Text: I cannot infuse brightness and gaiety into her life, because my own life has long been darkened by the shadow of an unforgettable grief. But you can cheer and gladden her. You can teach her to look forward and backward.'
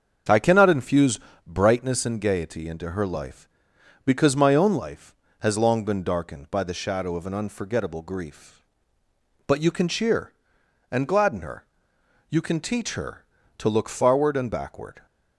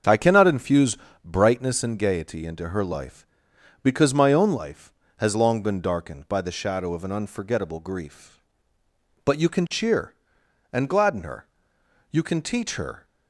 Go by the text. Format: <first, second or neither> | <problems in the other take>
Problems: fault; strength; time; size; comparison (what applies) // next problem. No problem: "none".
first | starts louder than the rest; until 1.3 s; 6.5 dB; also in the first // pauses between "infuse" and "brightness"; slight; at 0.9 s; 0.26 s long; slight in the first // stops before "to look forward and backward"; at 13.0 s